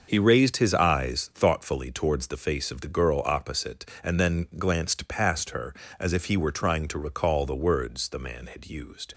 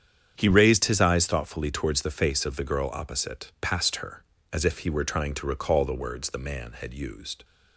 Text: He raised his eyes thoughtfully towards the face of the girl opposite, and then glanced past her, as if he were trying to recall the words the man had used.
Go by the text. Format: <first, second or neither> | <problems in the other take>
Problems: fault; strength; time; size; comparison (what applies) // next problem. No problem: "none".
first | starts louder than the rest; strong; until 1.3 s; 8 dB; also in the first // skips "and then glanced"; at 3.5 s